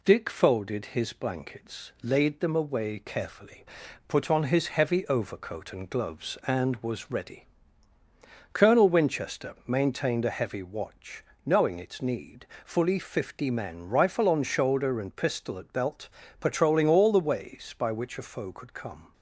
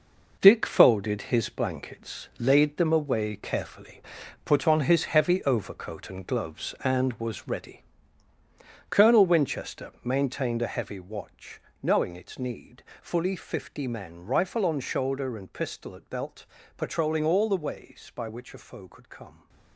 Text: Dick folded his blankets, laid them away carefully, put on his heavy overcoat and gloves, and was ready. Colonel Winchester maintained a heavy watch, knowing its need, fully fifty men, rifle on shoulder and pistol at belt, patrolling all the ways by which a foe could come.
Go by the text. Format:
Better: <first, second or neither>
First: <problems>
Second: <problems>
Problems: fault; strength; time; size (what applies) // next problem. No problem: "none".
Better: first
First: none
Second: gets quieter; strong; throughout; 8.5 dB